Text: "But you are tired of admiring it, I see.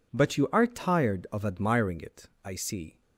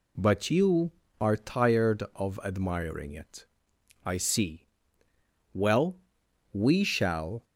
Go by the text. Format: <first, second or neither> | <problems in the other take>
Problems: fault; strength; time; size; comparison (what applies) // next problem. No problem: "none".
first | goes on to say "Well we shall"; strong; from 5.5 s on; 1.9 s long